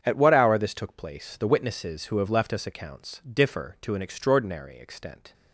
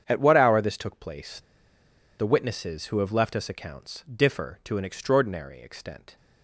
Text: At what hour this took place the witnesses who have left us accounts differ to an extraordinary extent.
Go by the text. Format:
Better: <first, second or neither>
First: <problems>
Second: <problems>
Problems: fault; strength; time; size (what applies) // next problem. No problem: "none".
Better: first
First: starts louder than the rest; strong; until 1.0 s; 8 dB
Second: starts louder than the rest; strong; until 1.0 s; 8 dB // pauses between "place" and "the"; noticeable; at 1.3 s; 0.77 s long